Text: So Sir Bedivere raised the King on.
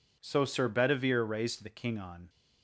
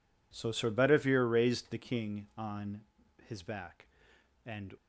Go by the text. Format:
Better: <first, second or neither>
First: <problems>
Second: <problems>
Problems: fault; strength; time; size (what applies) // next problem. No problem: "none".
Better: first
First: none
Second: goes on to say "his back and"; from 3.2 s on; 1.4 s long